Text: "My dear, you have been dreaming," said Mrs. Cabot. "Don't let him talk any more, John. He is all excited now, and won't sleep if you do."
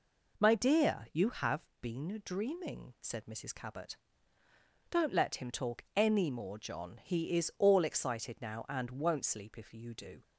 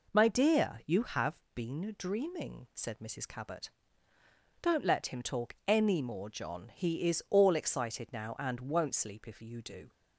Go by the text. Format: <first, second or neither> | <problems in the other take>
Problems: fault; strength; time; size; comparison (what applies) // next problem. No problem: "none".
neither | pauses between "have" and "been"; slight; the same in both